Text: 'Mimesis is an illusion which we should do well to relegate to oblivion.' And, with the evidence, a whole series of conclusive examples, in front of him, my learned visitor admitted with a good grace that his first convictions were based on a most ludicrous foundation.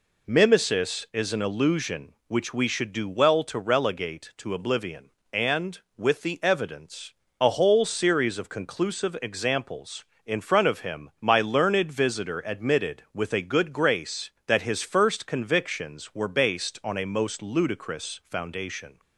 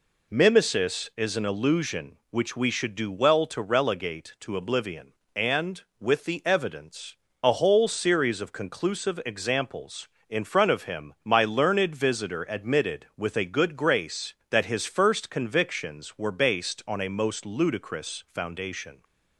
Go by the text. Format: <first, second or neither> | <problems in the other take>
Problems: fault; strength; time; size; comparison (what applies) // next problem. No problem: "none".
neither | none